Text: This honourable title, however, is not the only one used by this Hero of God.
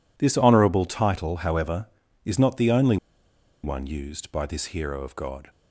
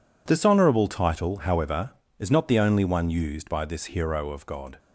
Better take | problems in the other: second | pauses between "only" and "one"; noticeable; at 2.9 s; 0.67 s long

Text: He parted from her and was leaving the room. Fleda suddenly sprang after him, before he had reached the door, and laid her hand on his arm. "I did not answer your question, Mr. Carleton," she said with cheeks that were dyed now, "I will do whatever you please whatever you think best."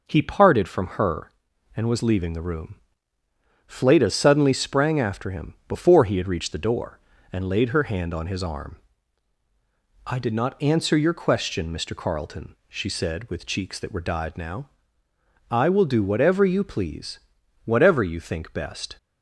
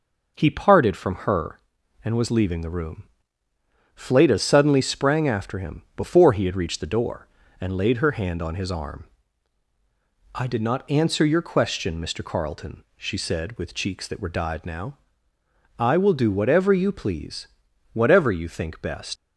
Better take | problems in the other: first | pauses between "please" and "whatever"; noticeable; at 17.4 s; 0.46 s long; noticeable in the first // leaves "best" unfinished; at 19.1 s; 95 ms

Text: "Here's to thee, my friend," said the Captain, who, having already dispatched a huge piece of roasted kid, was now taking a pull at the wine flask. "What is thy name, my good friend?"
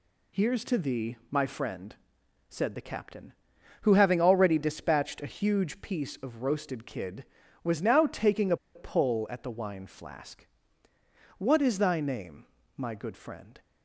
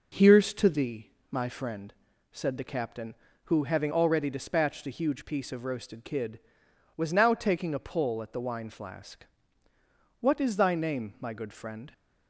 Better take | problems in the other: second | pauses between "a" and "pull"; slight; at 8.5 s; 0.18 s long

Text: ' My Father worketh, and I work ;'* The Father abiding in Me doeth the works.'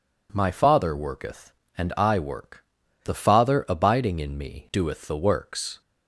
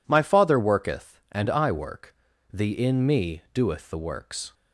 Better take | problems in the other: first | skips "Father abiding"; at 2.7 s

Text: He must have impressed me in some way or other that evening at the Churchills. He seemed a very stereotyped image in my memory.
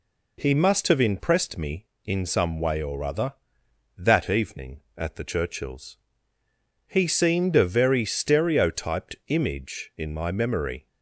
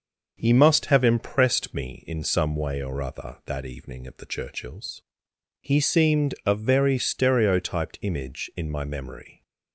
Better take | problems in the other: neither | none

